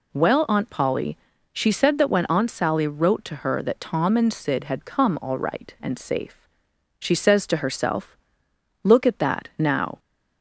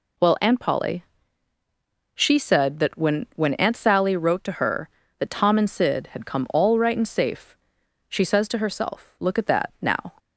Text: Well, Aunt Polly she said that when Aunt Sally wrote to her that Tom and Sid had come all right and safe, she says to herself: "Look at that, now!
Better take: first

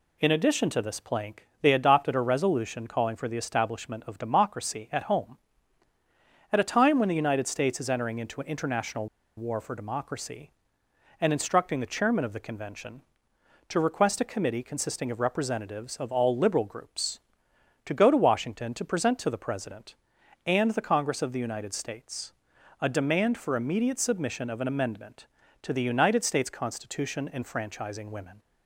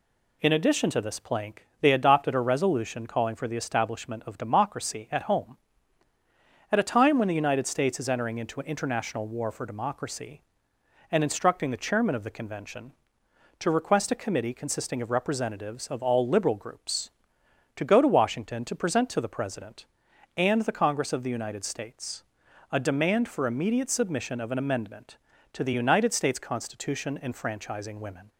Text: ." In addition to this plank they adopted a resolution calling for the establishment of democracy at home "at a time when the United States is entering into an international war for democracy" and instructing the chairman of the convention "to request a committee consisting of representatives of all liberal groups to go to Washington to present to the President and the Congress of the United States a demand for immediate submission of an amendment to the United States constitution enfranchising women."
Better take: second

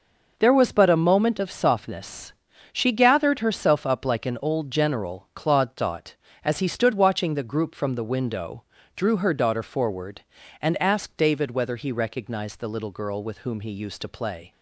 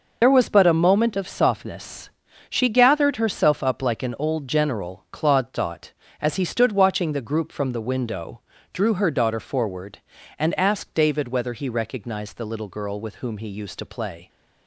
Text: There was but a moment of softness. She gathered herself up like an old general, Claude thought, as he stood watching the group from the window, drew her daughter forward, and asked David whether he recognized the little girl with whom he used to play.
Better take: first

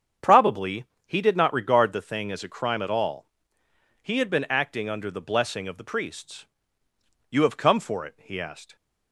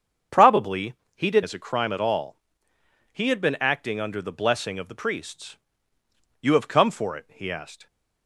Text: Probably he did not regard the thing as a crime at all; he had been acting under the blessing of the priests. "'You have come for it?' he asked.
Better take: first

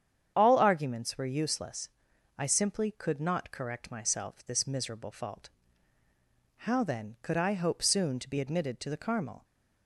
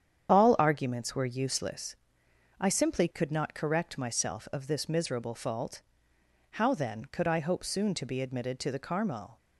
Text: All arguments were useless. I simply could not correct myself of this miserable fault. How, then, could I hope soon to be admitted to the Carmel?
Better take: second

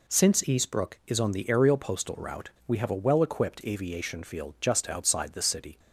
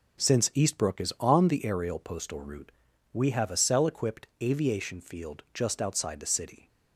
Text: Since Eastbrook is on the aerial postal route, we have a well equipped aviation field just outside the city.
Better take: first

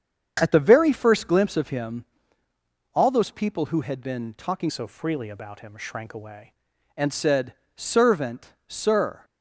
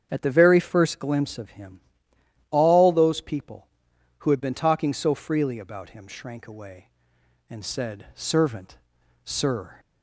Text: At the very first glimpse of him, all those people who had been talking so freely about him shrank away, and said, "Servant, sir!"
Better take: second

